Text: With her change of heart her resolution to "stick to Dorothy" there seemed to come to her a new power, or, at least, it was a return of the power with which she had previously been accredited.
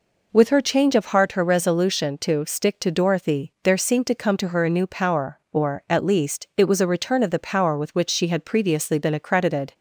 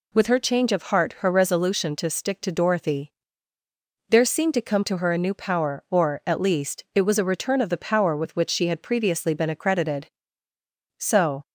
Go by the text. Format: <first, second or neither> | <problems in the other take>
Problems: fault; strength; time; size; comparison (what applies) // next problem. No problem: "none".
first | pauses between "Dorothy" and "there"; noticeable; at 3.1 s; 0.96 s long // goes on to say "So"; slight; from 10.9 s on; 0.48 s long